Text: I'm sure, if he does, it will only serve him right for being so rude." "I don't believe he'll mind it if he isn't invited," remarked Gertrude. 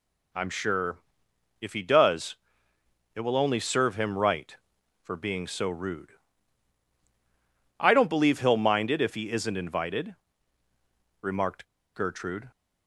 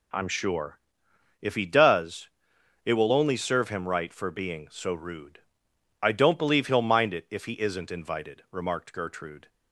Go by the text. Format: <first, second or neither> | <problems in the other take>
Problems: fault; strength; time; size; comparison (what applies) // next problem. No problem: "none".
second | pauses between "remarked" and "Gertrude"; slight; at 11.6 s; 0.29 s long